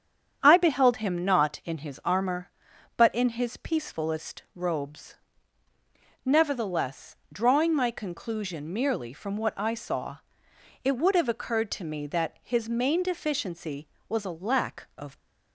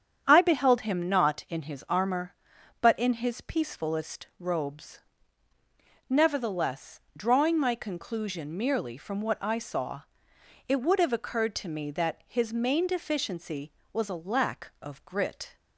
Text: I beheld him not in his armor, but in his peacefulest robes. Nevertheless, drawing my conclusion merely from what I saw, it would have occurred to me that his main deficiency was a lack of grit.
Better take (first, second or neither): second